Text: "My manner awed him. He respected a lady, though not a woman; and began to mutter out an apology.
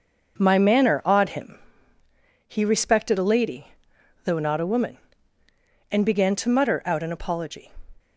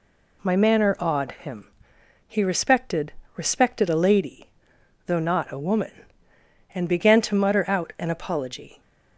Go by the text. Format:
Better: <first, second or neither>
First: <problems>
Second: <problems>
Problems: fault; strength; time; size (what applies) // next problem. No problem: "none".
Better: first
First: none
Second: says "respected" twice; at 3.3 s